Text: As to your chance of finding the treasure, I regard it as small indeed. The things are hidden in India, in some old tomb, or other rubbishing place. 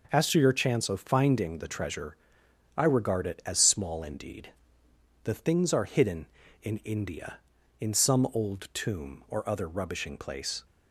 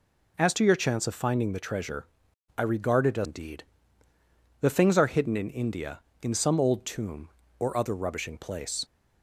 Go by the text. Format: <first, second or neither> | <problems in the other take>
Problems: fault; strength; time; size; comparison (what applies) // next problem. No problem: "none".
first | skips "small"; at 3.2 s